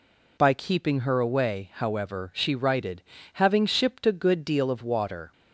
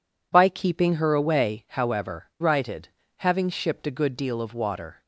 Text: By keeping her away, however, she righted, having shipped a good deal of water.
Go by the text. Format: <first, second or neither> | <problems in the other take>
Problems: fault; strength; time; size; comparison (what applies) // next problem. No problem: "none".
first | skips "she"; at 2.3 s